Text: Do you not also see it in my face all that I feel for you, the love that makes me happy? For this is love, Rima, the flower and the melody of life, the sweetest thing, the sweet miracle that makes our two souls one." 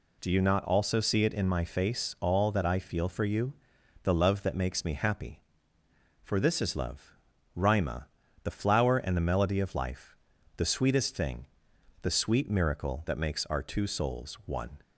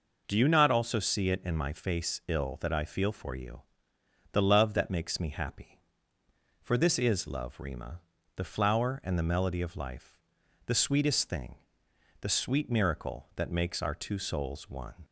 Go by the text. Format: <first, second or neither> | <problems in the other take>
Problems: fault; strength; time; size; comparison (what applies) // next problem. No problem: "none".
first | says "ill" for "all"; at 2.2 s